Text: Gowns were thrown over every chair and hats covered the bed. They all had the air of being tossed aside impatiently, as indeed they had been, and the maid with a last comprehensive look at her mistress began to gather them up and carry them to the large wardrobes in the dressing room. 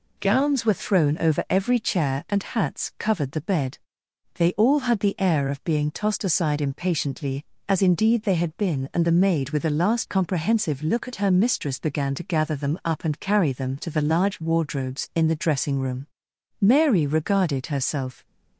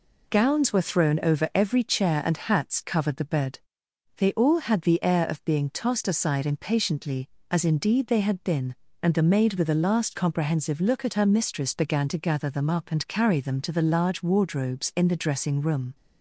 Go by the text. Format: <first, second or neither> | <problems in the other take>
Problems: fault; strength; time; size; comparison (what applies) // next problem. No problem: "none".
second | goes on to say "Mary regarded herself"; from 16.5 s on; 1.6 s long